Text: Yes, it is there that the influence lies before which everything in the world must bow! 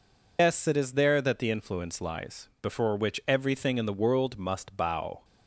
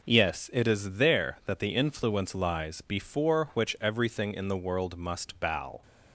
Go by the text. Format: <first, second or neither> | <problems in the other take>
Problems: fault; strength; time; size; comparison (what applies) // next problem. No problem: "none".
second | loses the start of "Yes"; at 0.3 s; 135 ms